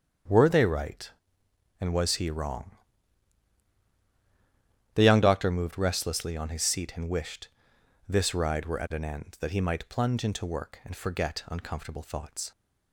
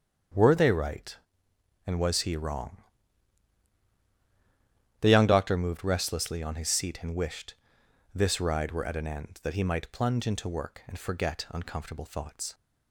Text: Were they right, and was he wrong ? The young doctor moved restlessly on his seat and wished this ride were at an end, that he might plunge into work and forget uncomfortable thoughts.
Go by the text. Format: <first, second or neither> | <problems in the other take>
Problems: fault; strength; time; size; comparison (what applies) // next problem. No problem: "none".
neither | starts louder than the rest; strong; the same in both // pauses between "wished" and "this"; noticeable; the same in both